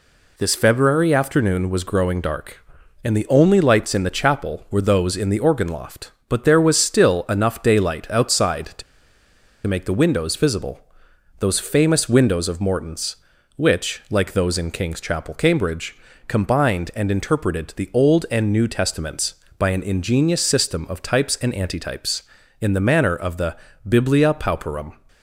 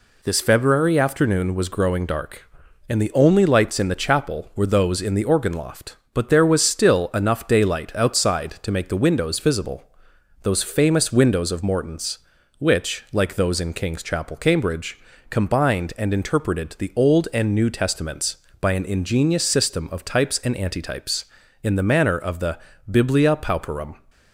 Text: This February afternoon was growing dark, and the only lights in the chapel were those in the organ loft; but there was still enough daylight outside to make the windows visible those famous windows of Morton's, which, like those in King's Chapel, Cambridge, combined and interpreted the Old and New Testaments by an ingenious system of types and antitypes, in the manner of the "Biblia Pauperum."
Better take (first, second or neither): second